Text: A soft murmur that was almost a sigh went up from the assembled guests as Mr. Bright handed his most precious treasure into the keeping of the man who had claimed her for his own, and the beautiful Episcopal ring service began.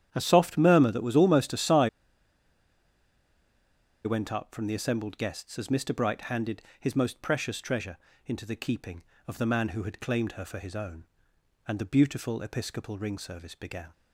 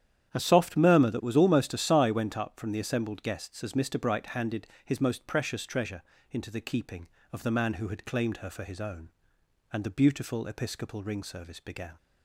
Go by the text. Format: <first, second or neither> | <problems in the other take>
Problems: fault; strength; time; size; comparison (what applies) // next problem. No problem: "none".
second | starts louder than the rest; strong; until 1.1 s; 9.5 dB; strong in the second // pauses between "sigh" and "went"; strong; at 1.8 s; 2.1 s long // pauses between "handed" and "his"; slight; at 6.5 s; 0.20 s long; slight in the second // pauses between "treasure" and "into"; slight; at 7.9 s; 0.28 s long; slight in the second